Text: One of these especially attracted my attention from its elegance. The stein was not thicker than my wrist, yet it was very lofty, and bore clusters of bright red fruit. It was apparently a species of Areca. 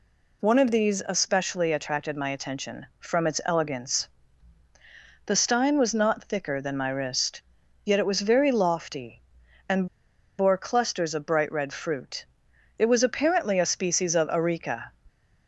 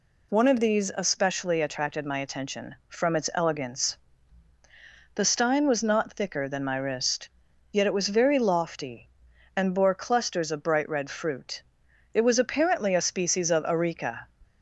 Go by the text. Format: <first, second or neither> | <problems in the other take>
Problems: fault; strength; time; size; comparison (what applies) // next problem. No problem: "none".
second | pauses between "and" and "bore"; noticeable; at 9.8 s; 0.52 s long